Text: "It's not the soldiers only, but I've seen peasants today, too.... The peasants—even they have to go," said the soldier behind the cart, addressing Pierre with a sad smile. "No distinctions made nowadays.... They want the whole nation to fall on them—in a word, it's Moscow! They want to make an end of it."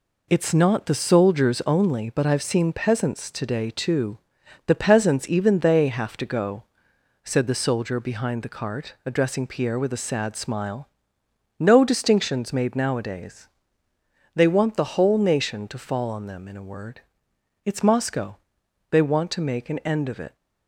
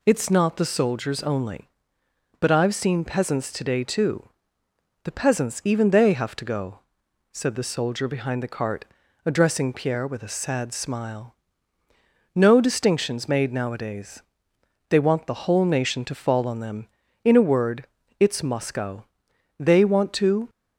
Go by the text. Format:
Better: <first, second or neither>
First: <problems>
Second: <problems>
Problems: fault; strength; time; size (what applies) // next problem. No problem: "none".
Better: first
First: none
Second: stops before "make an end of it"; at 20.4 s